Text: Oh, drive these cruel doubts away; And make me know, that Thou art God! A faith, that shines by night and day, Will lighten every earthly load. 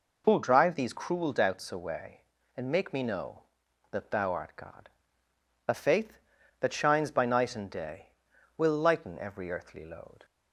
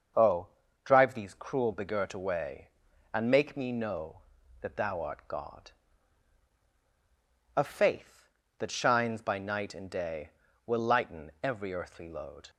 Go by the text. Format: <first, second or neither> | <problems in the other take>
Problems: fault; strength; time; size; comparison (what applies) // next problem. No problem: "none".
first | starts louder than the rest; until 1.5 s; 6.5 dB // says "begirt" for "doubts"; at 1.7 s